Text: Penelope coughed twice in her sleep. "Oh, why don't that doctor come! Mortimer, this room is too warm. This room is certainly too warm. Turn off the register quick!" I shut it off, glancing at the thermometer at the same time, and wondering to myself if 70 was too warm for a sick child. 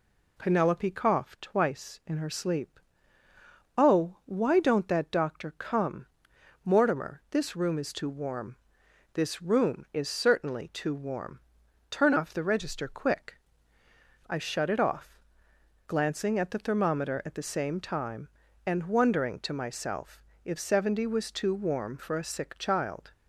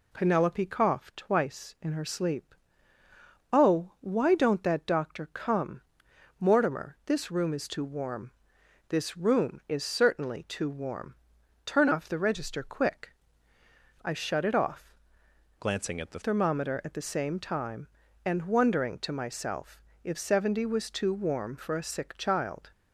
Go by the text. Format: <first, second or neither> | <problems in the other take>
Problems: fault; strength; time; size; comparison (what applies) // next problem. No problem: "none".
first | changes voice from "glancing" to "the"; from 15.5 to 16.1 s; 0.6 s long // pauses between "myself" and "if"; slight; at 19.8 s; 0.24 s long; slight in the first